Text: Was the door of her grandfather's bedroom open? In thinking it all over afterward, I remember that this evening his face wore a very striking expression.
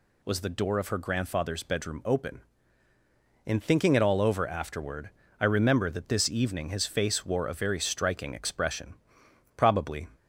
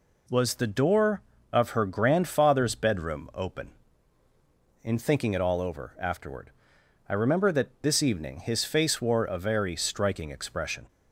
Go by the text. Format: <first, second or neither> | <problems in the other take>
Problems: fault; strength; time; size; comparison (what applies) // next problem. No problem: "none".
second | goes on to say "Probably"; from 9.5 s on; 0.52 s long